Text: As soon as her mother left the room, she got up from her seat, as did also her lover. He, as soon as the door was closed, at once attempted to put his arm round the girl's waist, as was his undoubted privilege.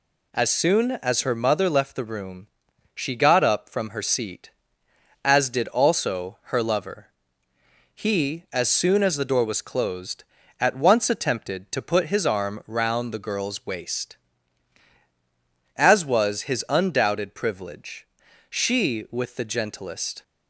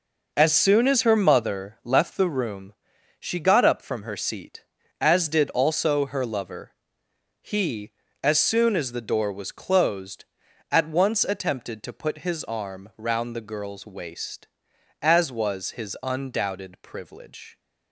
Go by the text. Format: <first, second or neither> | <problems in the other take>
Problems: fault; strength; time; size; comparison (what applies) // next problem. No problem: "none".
second | goes on to say "She with the gentlest"; strong; from 18.4 s on; 1.7 s long